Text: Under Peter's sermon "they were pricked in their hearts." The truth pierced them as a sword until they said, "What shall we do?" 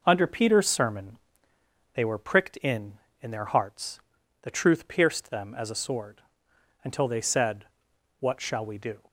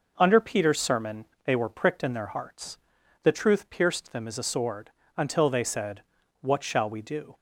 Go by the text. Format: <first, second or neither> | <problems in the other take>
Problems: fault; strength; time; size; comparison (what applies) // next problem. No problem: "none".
second | pauses between "sermon" and "they"; noticeable; at 1.1 s; 0.76 s long; slight in the second // says "in" twice; at 3.2 s // pauses between "sword" and "until"; noticeable; at 6.2 s; 0.60 s long; slight in the second